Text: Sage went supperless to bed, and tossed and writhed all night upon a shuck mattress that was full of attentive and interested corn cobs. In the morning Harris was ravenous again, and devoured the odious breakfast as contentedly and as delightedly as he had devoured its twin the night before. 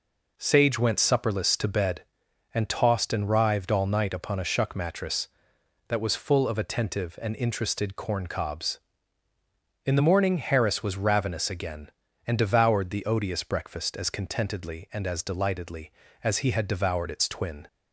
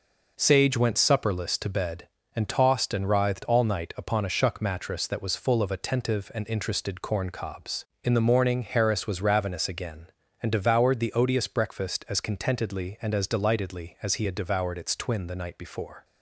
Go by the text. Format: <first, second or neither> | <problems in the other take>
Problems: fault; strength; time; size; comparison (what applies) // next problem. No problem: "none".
second | stops before "the night before"; at 17.6 s